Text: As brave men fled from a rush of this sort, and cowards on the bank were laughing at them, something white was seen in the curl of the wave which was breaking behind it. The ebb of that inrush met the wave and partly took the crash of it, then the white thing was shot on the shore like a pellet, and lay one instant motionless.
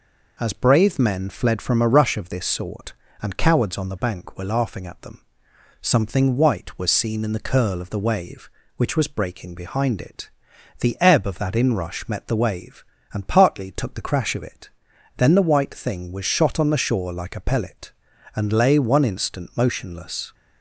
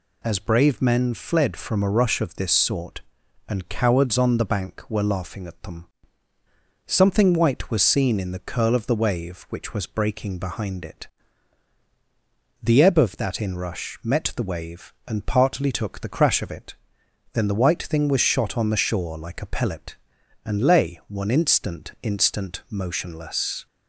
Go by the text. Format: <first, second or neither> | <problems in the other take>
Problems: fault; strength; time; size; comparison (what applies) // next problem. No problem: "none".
first | says "instant" twice; at 22.0 s